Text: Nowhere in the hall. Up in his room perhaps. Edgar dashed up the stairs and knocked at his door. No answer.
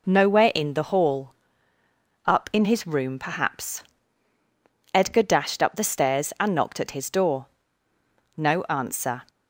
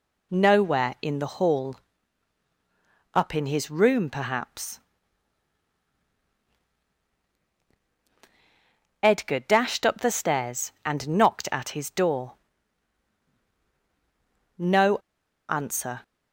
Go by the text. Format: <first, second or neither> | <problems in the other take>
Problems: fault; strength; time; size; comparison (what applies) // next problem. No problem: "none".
first | pauses between "No" and "answer"; noticeable; at 14.9 s; 0.51 s long